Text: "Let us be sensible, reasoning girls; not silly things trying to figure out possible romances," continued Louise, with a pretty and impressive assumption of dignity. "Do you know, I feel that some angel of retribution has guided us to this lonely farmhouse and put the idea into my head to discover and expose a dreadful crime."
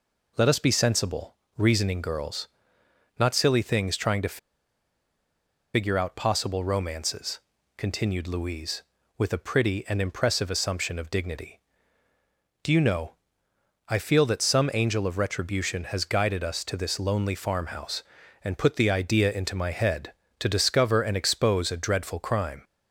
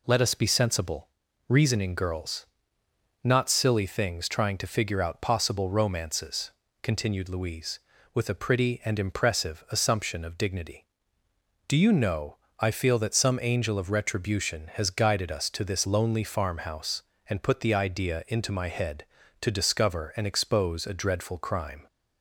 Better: second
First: pauses between "to" and "figure"; strong; at 4.3 s; 1.3 s long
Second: none

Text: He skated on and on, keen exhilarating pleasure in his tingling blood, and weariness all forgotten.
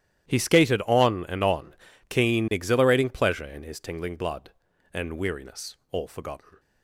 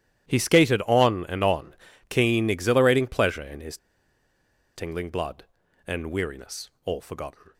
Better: first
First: starts louder than the rest; strong; until 1.3 s; 12 dB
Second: starts louder than the rest; strong; until 1.3 s; 12 dB // pauses between "his" and "tingling"; at 3.7 s; 0.98 s long

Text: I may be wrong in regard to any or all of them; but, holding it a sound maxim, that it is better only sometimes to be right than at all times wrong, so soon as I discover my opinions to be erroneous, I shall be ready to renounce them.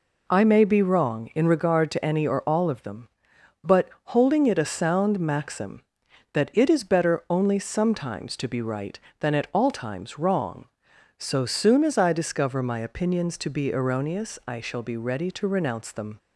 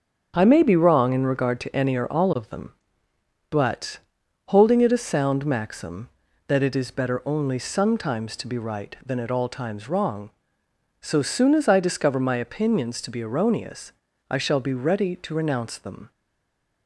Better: first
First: none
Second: starts louder than the rest; until 1.3 s; 7 dB // stays silent after the last word; slight; from 16.1 s on; 0.7 s long

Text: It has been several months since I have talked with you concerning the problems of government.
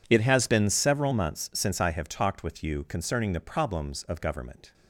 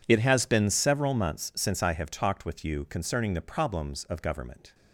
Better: neither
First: none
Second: none

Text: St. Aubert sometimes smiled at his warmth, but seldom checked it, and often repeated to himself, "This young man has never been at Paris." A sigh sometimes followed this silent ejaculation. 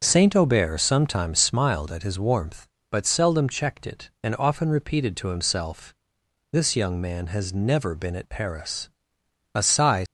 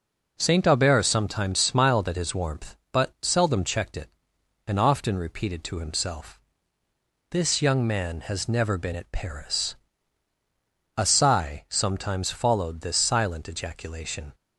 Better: second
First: starts louder than the rest; until 1.0 s; 6.5 dB // stops before "sometimes followed this silent ejaculation"; at 10.0 s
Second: none

